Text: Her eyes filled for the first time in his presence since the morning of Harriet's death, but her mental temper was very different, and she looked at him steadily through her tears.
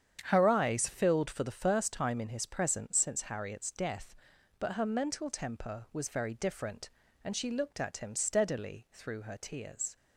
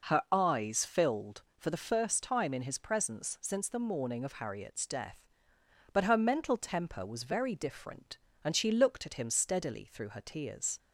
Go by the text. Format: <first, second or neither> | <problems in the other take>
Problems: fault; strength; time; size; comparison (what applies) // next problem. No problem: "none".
second | starts louder than the rest; strong; until 1.2 s; 8.5 dB // skips "the morning of"; at 3.2 s